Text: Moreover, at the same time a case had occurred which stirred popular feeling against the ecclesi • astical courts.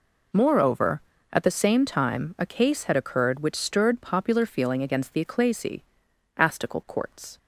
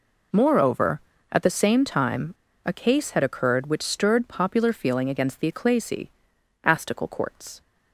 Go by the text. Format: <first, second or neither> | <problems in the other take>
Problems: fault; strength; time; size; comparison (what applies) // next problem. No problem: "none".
first | pauses between "time" and "a"; slight; at 2.3 s; 0.31 s long